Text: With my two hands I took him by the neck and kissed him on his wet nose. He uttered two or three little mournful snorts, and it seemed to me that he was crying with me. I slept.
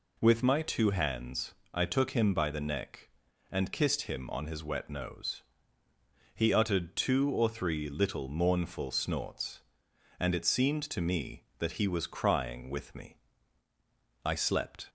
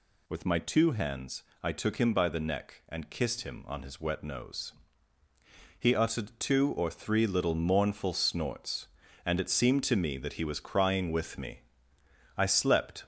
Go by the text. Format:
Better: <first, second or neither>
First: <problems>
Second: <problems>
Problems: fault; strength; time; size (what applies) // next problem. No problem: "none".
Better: first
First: pauses between "hands" and "I"; slight; at 1.5 s; 0.22 s long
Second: gets louder; noticeable; throughout; 4.5 dB // pauses between "hands" and "I"; slight; at 1.4 s; 0.18 s long